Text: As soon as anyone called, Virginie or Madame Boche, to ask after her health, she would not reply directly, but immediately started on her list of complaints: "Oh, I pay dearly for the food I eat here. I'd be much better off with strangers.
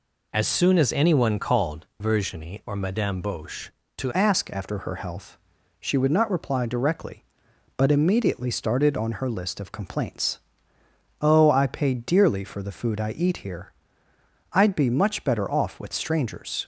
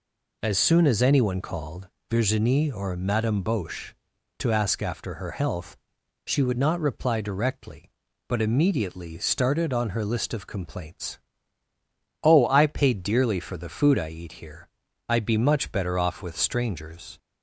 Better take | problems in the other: second | changes voice at "ask"; from 4.1 s on; 12.5 s long

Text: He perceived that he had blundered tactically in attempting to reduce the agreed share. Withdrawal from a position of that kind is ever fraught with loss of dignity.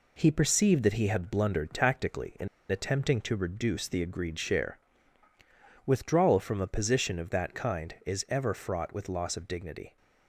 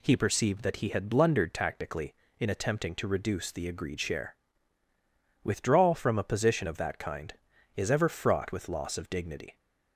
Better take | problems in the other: second | pauses between "in" and "attempting"; slight; at 2.4 s; 0.22 s long

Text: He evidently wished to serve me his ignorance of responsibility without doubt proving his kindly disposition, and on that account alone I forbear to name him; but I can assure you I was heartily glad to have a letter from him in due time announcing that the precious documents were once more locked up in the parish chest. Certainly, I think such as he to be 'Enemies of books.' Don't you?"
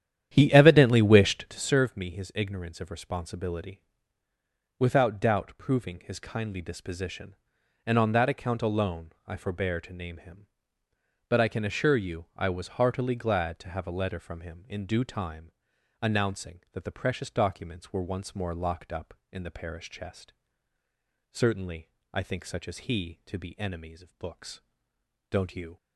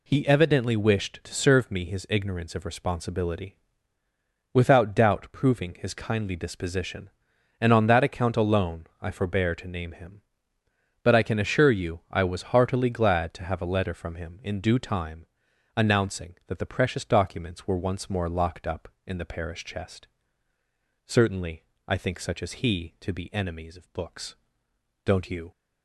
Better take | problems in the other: second | starts louder than the rest; strong; until 1.7 s; 10.5 dB // pauses between "responsibility" and "without"; noticeable; at 3.8 s; 0.96 s long; noticeable in the second // pauses between "time" and "announcing"; noticeable; at 15.5 s; 0.50 s long; noticeable in the second

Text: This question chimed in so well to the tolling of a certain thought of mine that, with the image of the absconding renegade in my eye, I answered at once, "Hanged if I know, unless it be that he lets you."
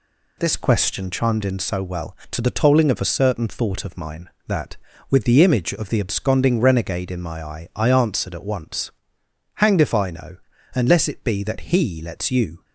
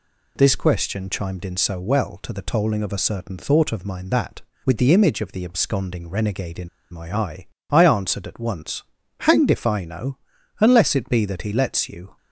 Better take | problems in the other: first | pauses between "in" and "my"; slight; at 6.6 s; 0.22 s long

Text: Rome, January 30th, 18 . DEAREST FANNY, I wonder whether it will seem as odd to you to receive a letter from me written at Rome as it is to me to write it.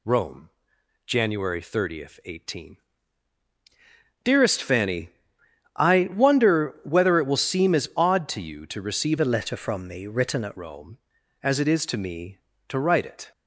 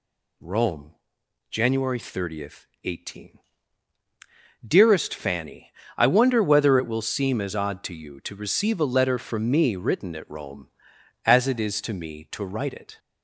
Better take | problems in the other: second | changes voice from "a" to "at"; from 9.1 to 10.5 s; 1.4 s long

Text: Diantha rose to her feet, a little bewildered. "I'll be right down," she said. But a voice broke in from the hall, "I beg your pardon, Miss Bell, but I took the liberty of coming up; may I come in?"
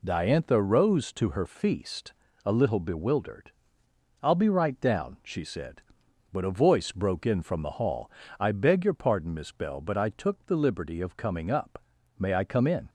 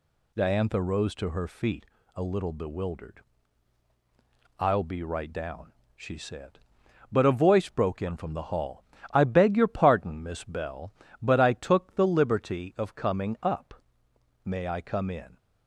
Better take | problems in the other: second | says "feast" for "feet"; at 1.4 s

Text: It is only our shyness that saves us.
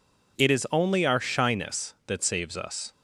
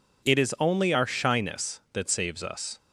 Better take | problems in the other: neither | none

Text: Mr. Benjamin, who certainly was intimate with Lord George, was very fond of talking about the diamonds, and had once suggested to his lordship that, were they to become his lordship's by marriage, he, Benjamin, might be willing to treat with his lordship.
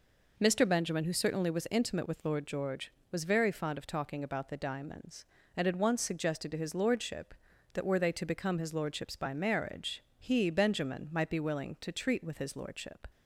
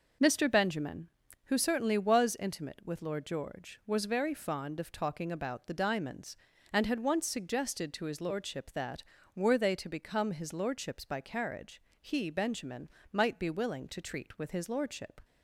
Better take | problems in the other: first | says "carriage" for "marriage"; at 11.2 s

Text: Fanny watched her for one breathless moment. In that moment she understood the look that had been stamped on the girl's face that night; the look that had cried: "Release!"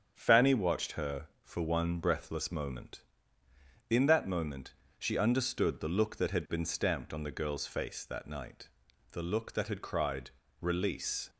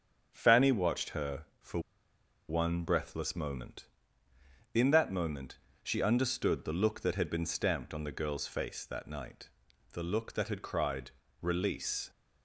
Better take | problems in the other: first | starts louder than the rest; strong; until 1.3 s; 8 dB; strong in the first // pauses between "for" and "one"; noticeable; at 1.7 s; 0.69 s long // pauses between "moment" and "she"; slight; at 5.5 s; 0.24 s long; slight in the first

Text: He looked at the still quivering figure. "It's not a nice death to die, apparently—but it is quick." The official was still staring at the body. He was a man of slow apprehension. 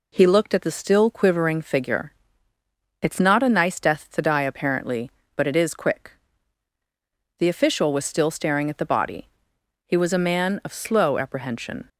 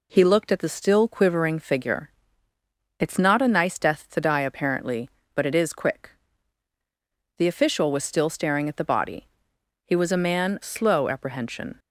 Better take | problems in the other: first | skips "of"; at 10.6 s

